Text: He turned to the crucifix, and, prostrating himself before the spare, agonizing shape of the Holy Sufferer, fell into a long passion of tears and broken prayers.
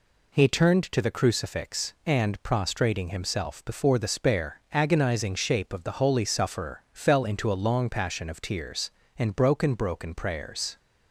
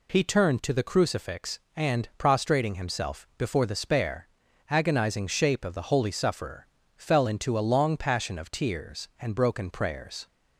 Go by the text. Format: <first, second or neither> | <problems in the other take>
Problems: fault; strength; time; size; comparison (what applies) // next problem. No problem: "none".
second | says "broken" twice; at 9.7 s